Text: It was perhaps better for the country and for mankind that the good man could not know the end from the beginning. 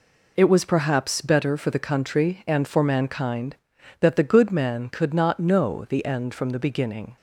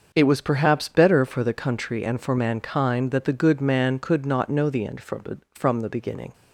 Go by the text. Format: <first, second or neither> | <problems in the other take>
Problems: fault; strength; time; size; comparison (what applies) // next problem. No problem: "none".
first | starts louder than the rest; until 1.1 s; 6 dB // says "from" twice; at 5.5 s